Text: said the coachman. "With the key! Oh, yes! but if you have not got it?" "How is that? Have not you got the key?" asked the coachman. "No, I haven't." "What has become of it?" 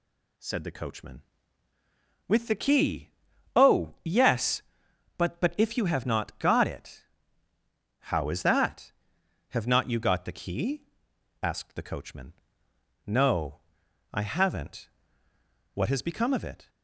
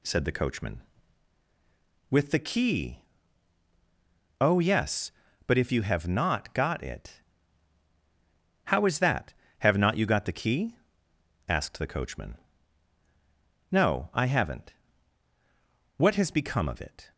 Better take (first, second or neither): second